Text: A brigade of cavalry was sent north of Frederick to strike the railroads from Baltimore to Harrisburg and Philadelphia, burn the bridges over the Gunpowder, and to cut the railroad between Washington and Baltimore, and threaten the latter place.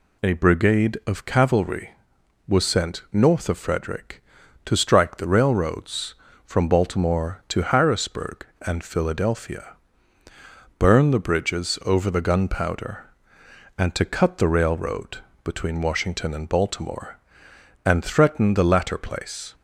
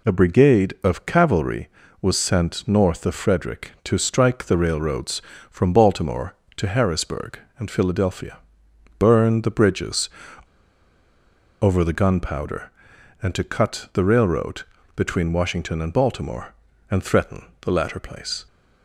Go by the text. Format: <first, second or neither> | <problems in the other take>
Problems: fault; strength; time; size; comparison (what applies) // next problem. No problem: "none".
first | pauses between "bridges" and "over"; strong; at 10.0 s; 1.5 s long // pauses between "railroad" and "between"; slight; at 14.6 s; 0.34 s long; slight in the first // pauses between "threaten" and "the"; slight; at 17.4 s; 0.16 s long